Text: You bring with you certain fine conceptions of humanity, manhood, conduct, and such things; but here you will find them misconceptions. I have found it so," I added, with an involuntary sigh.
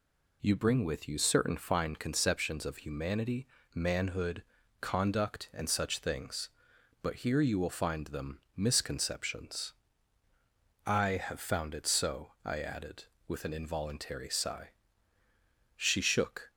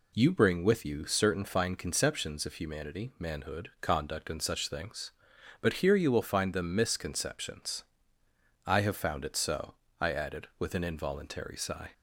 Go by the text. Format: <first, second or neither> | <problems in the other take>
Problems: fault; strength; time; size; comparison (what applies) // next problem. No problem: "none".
second | pauses between "them" and "misconceptions"; slight; at 8.3 s; 0.16 s long // goes on to say "She shook"; noticeable; from 15.7 s on; 0.74 s long